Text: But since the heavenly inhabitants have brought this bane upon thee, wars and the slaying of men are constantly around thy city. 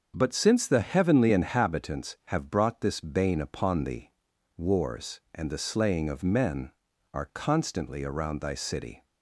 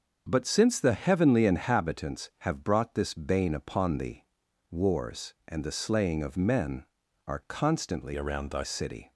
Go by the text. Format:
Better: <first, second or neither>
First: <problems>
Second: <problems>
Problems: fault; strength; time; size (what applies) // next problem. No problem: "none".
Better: first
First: starts louder than the rest; until 1.1 s; 7 dB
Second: starts louder than the rest; until 1.3 s; 6.5 dB // changes voice from "around" to "thy"; from 8.1 to 8.6 s; 0.5 s long